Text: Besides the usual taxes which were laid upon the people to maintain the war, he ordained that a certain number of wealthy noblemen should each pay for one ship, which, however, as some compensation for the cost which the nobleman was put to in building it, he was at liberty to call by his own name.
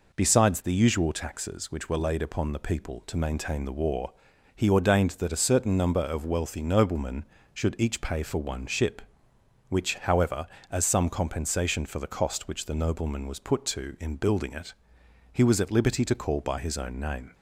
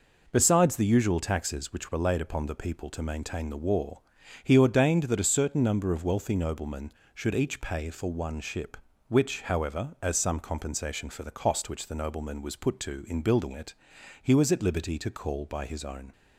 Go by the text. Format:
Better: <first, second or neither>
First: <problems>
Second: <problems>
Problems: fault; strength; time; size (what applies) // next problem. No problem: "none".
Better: first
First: none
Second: stops before "name"; at 16.1 s